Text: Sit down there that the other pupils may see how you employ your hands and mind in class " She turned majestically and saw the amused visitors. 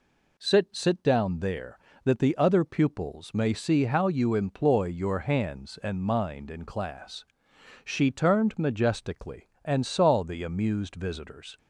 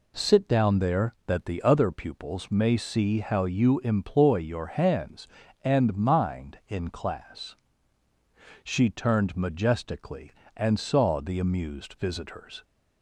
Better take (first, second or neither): second